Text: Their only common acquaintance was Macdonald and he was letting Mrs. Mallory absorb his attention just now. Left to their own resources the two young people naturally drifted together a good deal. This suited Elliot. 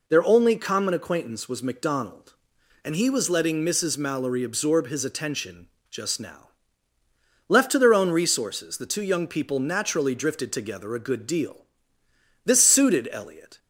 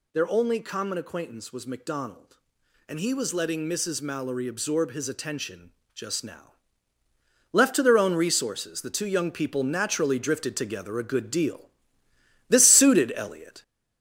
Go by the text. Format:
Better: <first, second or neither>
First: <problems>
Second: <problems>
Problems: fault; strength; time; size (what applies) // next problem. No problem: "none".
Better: first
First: pauses between "attention" and "just"; slight; at 5.6 s; 0.24 s long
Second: gets louder; noticeable; throughout; 4.5 dB // pauses between "attention" and "just"; slight; at 5.7 s; 0.24 s long